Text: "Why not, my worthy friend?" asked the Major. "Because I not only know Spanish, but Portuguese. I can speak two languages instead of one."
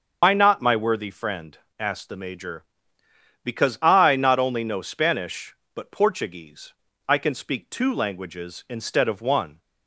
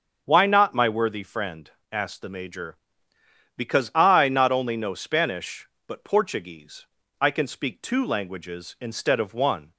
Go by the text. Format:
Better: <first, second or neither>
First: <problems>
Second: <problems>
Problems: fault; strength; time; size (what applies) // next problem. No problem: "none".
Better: second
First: loses the start of "Why"; at 0.2 s; 100 ms // starts louder than the rest; until 1.2 s; 6 dB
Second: starts louder than the rest; until 1.2 s; 7 dB